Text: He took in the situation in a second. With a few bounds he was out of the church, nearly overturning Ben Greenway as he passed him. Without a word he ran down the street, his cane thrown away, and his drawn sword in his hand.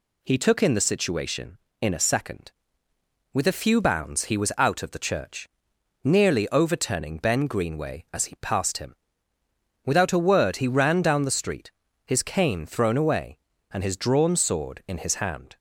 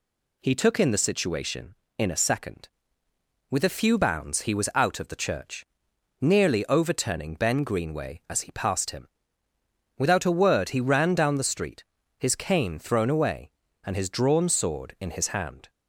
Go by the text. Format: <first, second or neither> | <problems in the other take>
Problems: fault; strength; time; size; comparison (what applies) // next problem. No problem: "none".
neither | none